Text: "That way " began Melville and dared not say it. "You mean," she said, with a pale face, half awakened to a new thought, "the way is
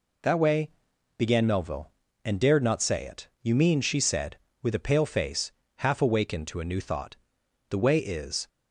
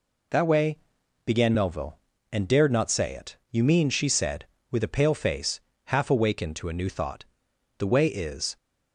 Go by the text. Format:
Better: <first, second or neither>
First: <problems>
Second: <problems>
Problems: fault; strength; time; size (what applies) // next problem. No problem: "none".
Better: neither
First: none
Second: none